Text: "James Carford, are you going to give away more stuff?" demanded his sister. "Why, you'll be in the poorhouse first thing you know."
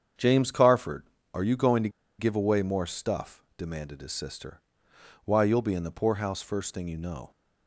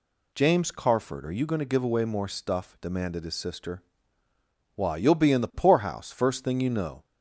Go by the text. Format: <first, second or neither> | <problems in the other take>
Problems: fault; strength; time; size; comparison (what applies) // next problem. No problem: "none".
second | starts louder than the rest; strong; until 1.4 s; 7.5 dB // pauses between "to" and "give"; slight; at 1.8 s; 0.29 s long